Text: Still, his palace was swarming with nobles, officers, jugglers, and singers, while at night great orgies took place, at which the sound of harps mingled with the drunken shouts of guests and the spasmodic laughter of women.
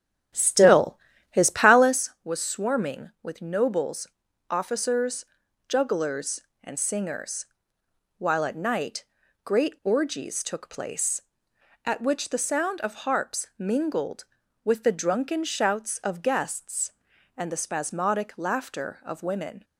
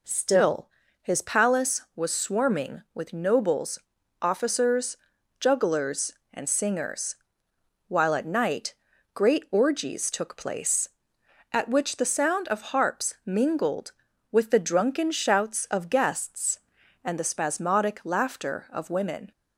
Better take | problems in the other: second | starts louder than the rest; strong; until 2.0 s; 9 dB // pauses between "night" and "great"; at 9.0 s; 0.40 s long; also in the second

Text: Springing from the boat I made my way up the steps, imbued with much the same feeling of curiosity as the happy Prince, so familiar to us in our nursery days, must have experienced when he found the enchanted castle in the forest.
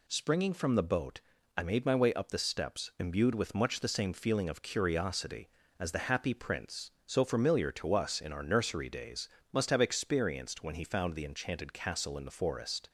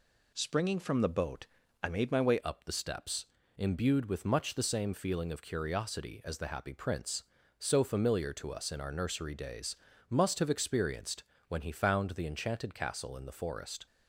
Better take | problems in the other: first | pauses between "boat" and "I"; slight; at 1.4 s; 0.36 s long; slight in the first // changes voice at "up"; from 2.4 s on; 11.4 s long // pauses between "experienced" and "when"; slight; at 11.2 s; 0.24 s long

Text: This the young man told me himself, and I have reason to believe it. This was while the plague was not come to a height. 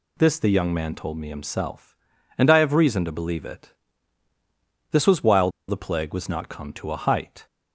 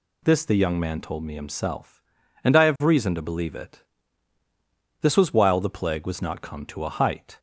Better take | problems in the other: second | pauses between "while" and "the"; slight; at 5.4 s; 0.19 s long

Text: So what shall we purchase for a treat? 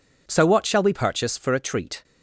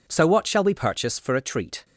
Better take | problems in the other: neither | none

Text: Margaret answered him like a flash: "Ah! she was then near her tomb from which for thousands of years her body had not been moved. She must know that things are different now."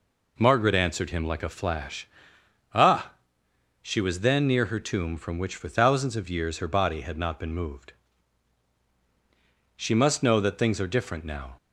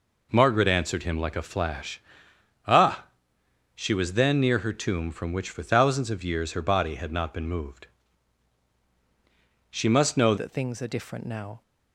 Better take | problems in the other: first | changes voice at "that"; from 10.3 s on; 1.3 s long

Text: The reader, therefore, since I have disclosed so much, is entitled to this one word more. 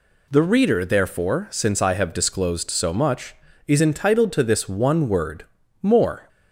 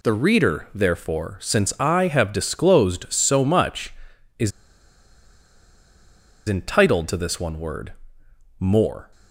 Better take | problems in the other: first | pauses between "is" and "entitled"; strong; at 4.5 s; 1.9 s long // pauses between "word" and "more"; noticeable; at 7.9 s; 0.66 s long; also in the first

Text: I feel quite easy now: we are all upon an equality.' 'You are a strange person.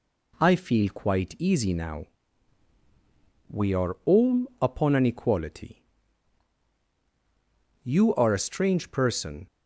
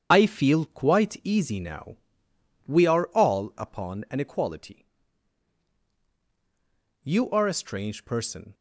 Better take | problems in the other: first | loses the start of "I"; at 0.1 s; 80 ms // starts louder than the rest; strong; until 1.1 s; 8 dB

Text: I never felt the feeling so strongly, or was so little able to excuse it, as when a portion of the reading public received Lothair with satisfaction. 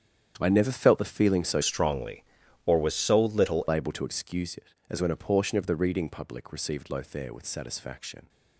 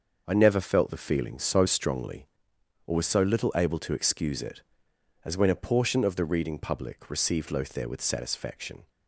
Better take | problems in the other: second | starts louder than the rest; strong; until 1.3 s; 8.5 dB; noticeable in the second // changes voice from "strongly" to "little"; from 1.6 to 3.6 s; 2.0 s long

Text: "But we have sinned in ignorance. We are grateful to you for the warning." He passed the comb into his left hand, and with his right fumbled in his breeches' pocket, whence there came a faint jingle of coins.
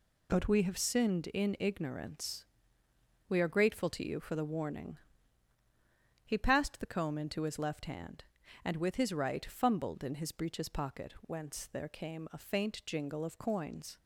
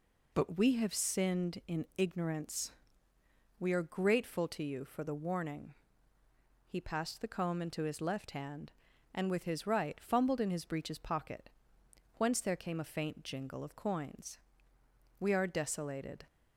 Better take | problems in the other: first | goes on to say "We are desolated"; noticeable; from 15.2 s on; 1.0 s long

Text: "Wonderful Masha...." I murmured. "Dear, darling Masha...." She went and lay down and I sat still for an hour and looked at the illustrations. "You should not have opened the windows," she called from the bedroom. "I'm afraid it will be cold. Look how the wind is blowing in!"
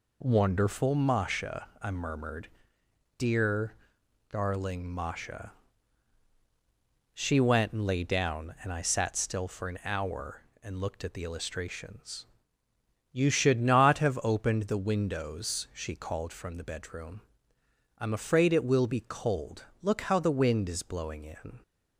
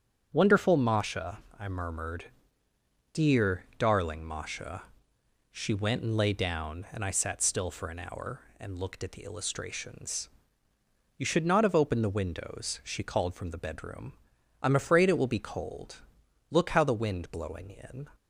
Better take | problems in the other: first | starts louder than the rest; strong; until 1.3 s; 8 dB // skips "is"; at 17.3 s

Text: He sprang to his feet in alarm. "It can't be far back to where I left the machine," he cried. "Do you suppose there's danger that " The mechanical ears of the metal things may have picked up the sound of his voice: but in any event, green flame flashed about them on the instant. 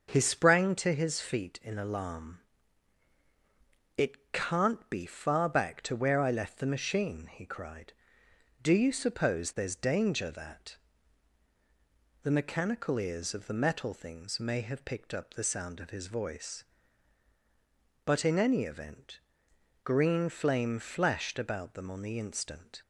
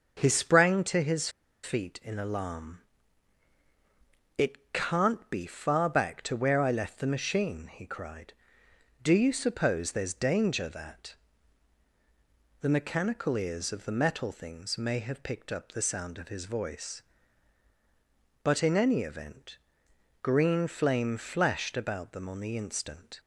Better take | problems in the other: first | starts louder than the rest; until 1.2 s; 6.5 dB; also in the first // pauses between "his" and "feet"; slight; at 1.2 s; 0.33 s long

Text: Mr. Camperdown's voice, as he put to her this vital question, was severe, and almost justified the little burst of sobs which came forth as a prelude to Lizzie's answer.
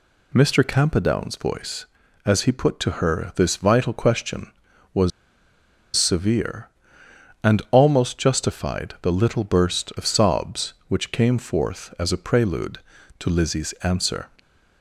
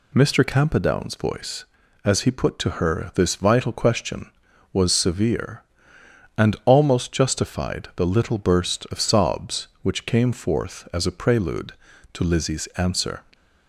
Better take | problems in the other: second | pauses between "was" and "severe"; noticeable; at 5.1 s; 0.85 s long

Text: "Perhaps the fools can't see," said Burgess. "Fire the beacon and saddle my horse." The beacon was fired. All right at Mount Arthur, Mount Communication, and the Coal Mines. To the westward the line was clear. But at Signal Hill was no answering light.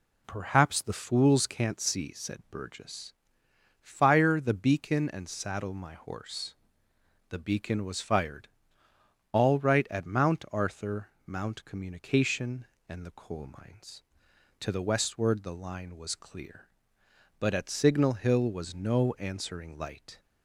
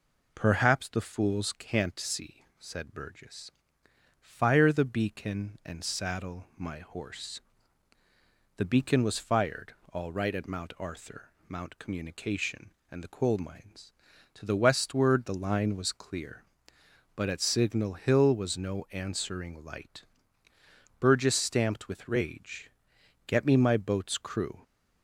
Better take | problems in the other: first | goes on to say "Burgess stamped with rage Get me my boat's crew"; strong; from 21.0 s on; 3.6 s long

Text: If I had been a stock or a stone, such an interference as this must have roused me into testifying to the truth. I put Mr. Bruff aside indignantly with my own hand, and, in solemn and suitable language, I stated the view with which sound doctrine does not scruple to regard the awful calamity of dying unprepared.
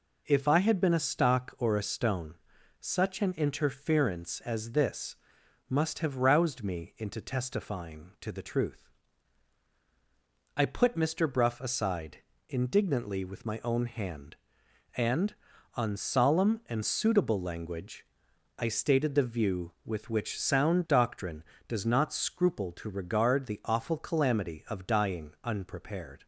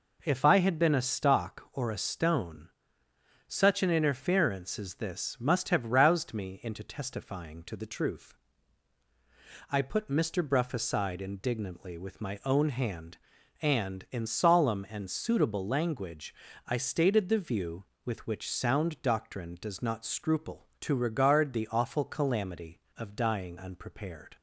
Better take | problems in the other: second | pauses between "this" and "must"; noticeable; at 5.1 s; 0.52 s long // pauses between "aside" and "indignantly"; slight; at 12.1 s; 0.28 s long // says "on" for "in"; at 15.7 s

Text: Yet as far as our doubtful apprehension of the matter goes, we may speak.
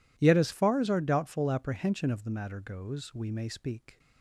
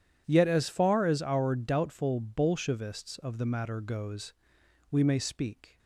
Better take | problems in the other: first | says "bolshevists" for "apprehension"; at 2.1 s

